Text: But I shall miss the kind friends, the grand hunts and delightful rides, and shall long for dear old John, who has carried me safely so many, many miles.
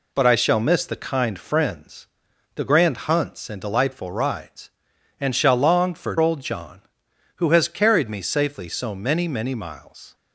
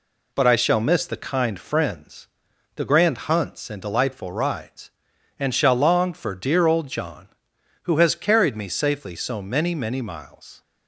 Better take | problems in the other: second | skips "dear"; at 6.1 s

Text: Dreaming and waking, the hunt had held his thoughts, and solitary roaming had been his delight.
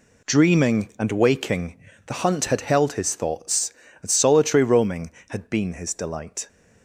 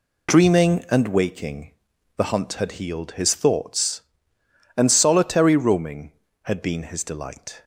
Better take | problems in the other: first | says "healed" for "held"; at 2.7 s

